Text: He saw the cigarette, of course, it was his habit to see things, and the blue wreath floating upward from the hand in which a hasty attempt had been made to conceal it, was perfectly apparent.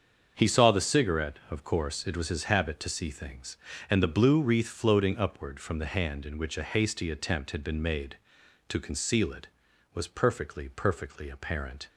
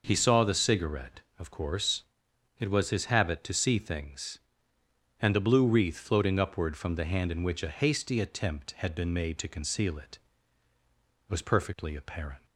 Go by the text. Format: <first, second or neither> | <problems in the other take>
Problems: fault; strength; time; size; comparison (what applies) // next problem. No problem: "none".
second | starts louder than the rest; until 1.3 s; 7 dB // says "perfectly" twice; at 10.6 s